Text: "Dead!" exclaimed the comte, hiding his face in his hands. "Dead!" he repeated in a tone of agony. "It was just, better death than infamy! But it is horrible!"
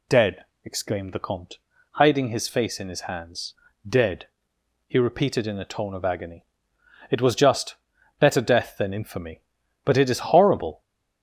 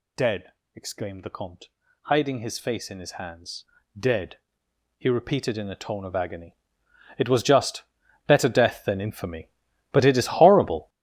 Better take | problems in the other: first | gets louder; strong; throughout; 11.5 dB

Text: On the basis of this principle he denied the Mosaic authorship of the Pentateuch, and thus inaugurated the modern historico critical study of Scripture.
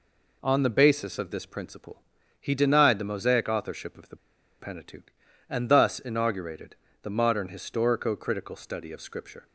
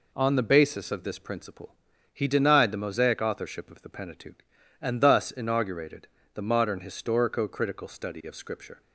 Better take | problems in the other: second | pauses between "principle" and "he"; at 2.0 s; 0.38 s long; also in the second // pauses between "the" and "Pentateuch"; at 4.1 s; 0.43 s long // pauses between "inaugurated" and "the"; slight; at 6.7 s; 0.28 s long; slight in the second

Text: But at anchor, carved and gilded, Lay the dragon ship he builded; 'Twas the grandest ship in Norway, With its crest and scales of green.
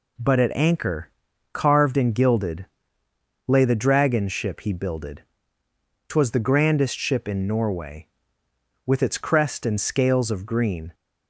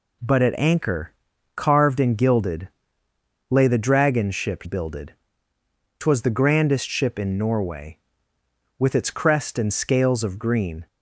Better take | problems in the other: first | skips "he"; at 4.6 s

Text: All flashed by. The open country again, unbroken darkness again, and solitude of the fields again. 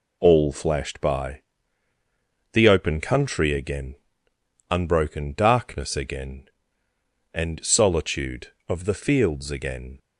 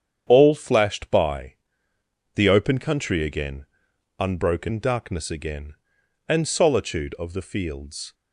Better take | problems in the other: first | starts louder than the rest; strong; until 1.2 s; 8.5 dB // stops before "again"; at 8.1 s

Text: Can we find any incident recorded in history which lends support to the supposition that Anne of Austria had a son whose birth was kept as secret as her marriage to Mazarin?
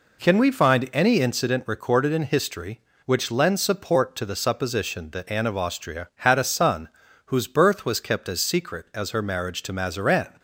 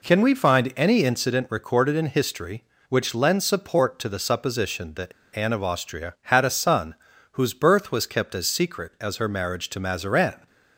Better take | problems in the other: first | pauses between "that" and "Anne"; slight; at 5.1 s; 0.23 s long // pauses between "son" and "whose"; at 6.9 s; 0.38 s long; also in the first

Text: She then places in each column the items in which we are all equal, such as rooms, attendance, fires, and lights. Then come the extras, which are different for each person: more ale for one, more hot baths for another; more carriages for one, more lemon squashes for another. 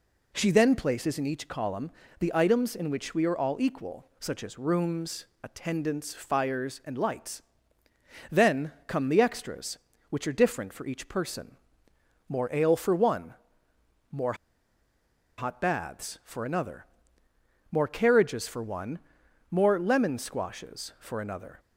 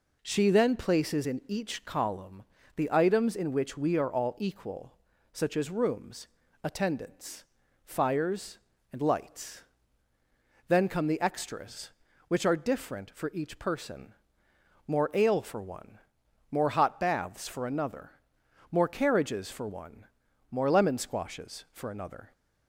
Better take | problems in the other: second | pauses between "column" and "the"; slight; at 1.9 s; 0.28 s long; slight in the second // pauses between "more" and "hot"; at 14.3 s; 1.0 s long

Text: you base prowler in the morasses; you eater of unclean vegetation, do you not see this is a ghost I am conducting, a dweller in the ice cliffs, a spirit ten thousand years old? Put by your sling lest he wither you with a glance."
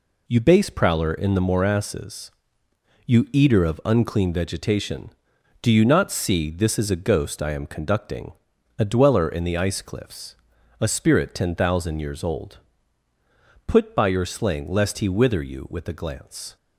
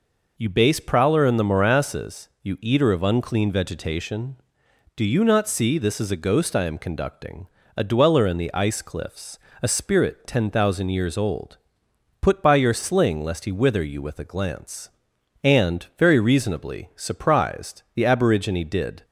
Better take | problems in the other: first | goes on to say "And very reasonably surprised the aborigine did"; strong; from 15.4 s on; 3.6 s long

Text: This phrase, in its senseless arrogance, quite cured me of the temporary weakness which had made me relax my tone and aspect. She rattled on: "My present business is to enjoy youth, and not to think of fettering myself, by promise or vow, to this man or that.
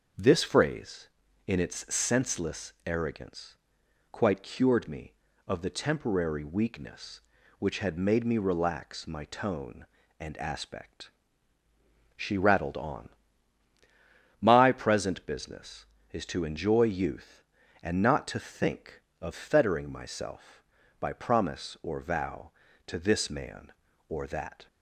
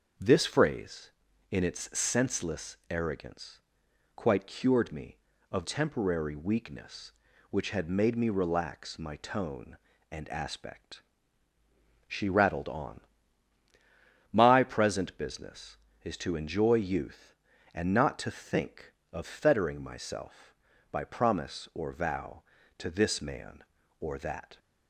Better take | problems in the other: first | starts louder than the rest; noticeable; until 1.5 s; 6 dB; noticeable in the first // skips "the"; at 5.6 s

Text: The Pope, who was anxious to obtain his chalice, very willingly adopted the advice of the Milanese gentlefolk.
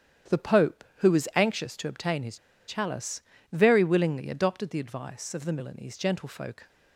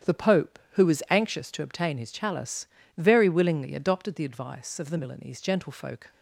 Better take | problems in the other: second | starts louder than the rest; strong; until 1.5 s; 9.5 dB; strong in the second // pauses between "his" and "chalice"; slight; at 2.3 s; 0.31 s long

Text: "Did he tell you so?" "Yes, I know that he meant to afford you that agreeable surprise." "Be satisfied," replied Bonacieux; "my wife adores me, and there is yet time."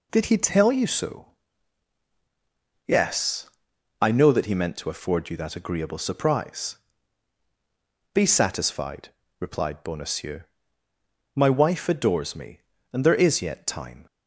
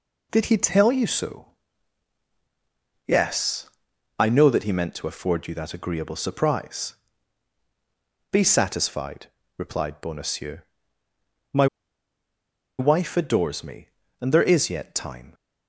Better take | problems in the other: first | pauses between "my" and "wife"; at 11.6 s; 1.1 s long

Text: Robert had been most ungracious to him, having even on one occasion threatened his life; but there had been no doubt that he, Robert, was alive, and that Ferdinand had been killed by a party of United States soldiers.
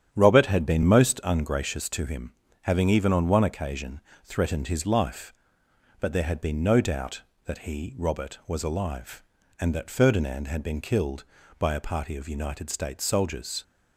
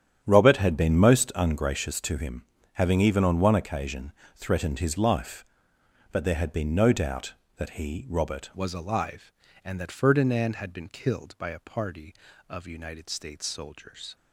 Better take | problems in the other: first | starts louder than the rest; strong; until 1.2 s; 10 dB; strong in the first // pauses between "occasion" and "threatened"; slight; at 4.1 s; 0.24 s long; slight in the first // changes voice at "was"; from 8.5 s on; 5.6 s long

